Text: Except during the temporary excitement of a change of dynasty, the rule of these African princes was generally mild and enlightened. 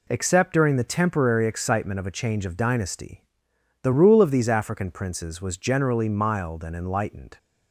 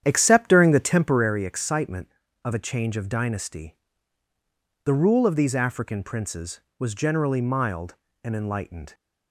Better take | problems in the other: first | starts louder than the rest; strong; until 1.4 s; 9.5 dB

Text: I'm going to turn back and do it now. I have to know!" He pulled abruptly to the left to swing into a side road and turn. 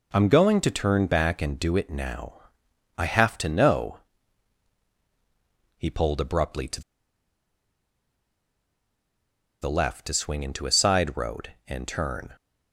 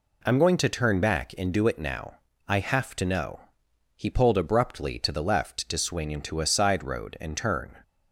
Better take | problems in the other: second | pauses between "to" and "the"; strong; at 6.8 s; 2.7 s long

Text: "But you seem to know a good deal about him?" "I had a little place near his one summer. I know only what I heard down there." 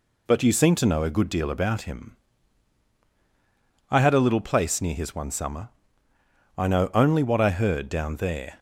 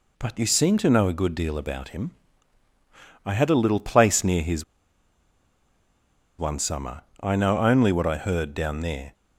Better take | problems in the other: first | pauses between "his" and "one"; strong; at 4.6 s; 1.7 s long

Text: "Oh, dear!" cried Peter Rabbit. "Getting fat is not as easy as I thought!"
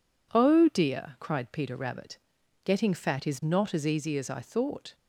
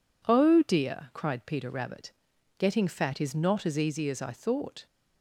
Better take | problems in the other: neither | none

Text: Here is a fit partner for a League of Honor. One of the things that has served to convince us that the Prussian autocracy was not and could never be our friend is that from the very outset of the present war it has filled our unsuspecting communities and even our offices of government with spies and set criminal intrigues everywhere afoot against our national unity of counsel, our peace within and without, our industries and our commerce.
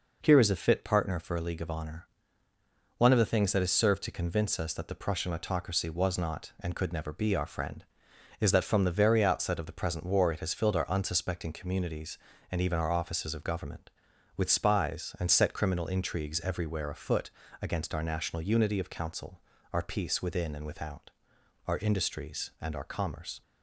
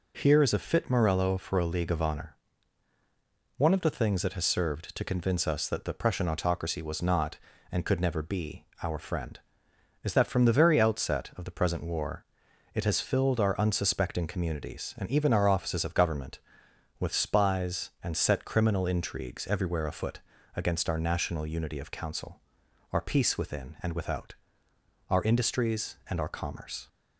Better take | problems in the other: first | says "morello" for "partner"; at 0.8 s // pauses between "be" and "our"; slight; at 8.6 s; 0.18 s long // pauses between "war" and "it"; noticeable; at 12.2 s; 0.50 s long // pauses between "afoot" and "against"; slight; at 20.1 s; 0.36 s long; slight in the first

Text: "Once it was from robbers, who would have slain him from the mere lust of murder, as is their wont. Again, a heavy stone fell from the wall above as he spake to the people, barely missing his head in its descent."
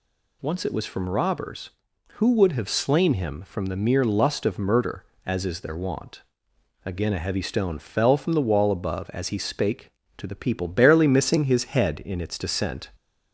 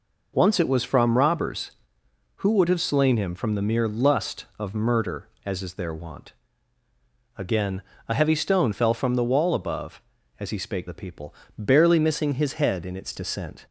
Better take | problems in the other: first | skips "to"; at 10.8 s

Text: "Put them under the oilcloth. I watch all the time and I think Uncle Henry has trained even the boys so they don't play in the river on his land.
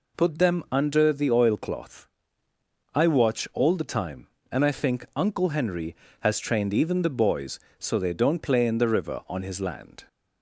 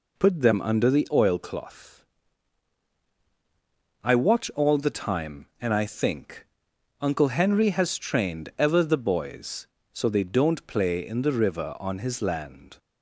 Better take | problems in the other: first | pauses between "think" and "Uncle"; noticeable; at 6.4 s; 0.54 s long // says "ever" for "even"; at 8.5 s

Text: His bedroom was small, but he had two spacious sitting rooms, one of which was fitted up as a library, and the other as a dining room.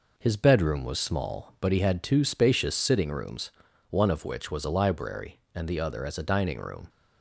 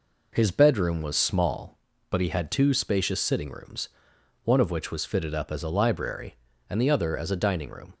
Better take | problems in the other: second | skips "fitted up as"; at 4.6 s

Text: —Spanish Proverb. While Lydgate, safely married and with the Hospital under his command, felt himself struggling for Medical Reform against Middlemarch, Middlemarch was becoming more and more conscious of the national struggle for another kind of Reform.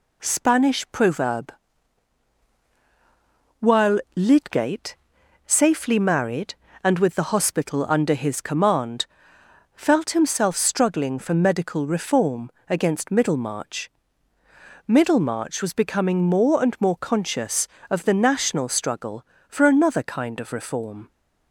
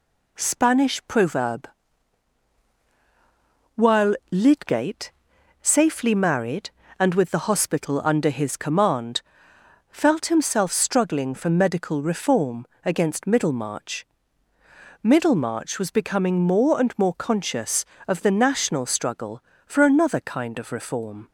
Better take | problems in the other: neither | pauses between "Reform" and "against"; slight; the same in both

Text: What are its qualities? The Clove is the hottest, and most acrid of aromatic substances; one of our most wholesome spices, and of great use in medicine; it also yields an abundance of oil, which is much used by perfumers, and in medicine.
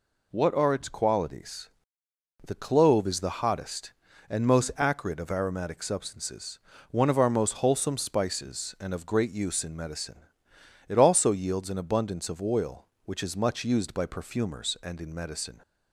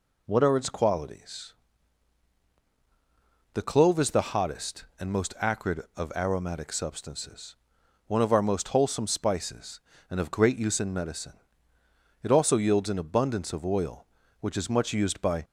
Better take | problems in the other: first | stops before "perfumers and in medicine"; at 15.4 s

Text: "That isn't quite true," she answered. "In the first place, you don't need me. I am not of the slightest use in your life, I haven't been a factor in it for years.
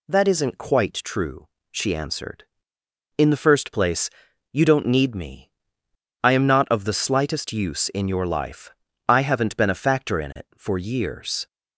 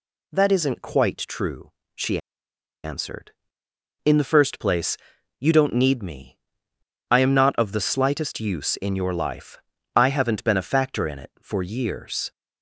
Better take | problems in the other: first | pauses between "she" and "answered"; noticeable; at 2.1 s; 0.64 s long

